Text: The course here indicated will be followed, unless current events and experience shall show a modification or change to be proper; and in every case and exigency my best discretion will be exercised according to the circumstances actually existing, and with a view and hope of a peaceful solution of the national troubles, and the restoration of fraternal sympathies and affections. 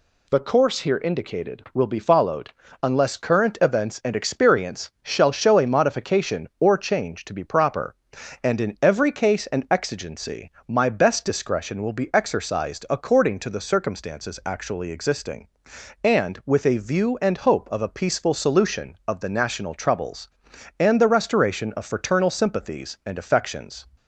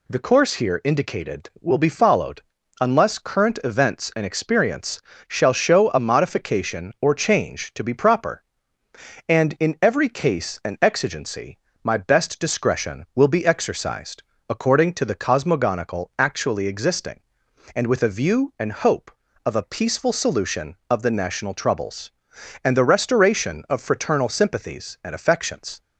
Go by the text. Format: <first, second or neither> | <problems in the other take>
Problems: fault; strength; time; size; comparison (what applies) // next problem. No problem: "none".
first | pauses between "experience" and "shall"; slight; at 5.0 s; 0.26 s long // pauses between "exigency" and "my"; slight; at 11.5 s; 0.26 s long; slight in the first // pauses between "exercised" and "according"; slight; at 14.2 s; 0.24 s long // says "cosmogonical" for "circumstances"; at 15.1 s